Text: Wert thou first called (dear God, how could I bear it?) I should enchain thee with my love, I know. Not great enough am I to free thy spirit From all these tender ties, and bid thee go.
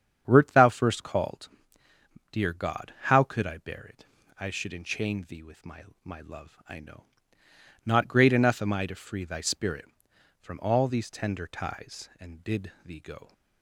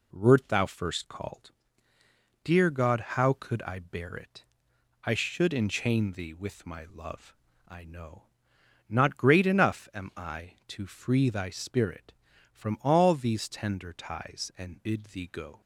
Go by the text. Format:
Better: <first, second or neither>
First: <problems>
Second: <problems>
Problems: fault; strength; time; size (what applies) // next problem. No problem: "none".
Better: second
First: starts louder than the rest; strong; until 1.3 s; 8 dB // says "my" twice; at 6.0 s // pauses between "bid" and "thee"; slight; at 12.7 s; 0.16 s long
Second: none